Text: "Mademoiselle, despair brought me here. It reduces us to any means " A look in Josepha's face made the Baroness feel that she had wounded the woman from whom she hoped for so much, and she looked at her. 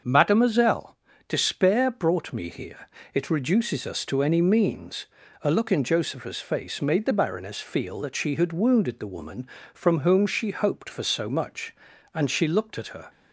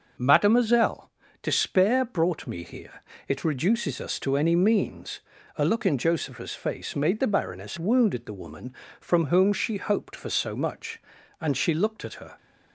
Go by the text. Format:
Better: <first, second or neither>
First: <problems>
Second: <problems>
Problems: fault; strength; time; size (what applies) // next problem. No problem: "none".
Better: first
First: starts louder than the rest; until 1.3 s; 6.5 dB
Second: starts louder than the rest; until 1.4 s; 6.5 dB // skips "feel that she had"; at 7.7 s